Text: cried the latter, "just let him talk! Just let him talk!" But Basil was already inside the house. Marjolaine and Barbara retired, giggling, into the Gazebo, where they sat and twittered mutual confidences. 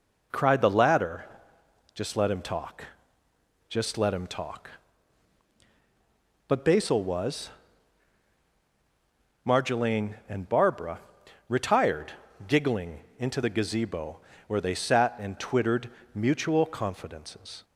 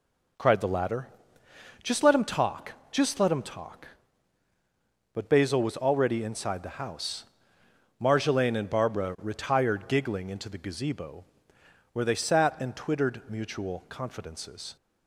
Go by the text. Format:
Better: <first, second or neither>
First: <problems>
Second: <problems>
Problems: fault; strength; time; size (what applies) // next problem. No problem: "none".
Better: second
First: skips "already inside the house"; at 8.4 s // pauses between "Barbara" and "retired"; noticeable; at 10.9 s; 0.50 s long // pauses between "twittered" and "mutual"; slight; at 15.8 s; 0.24 s long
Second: none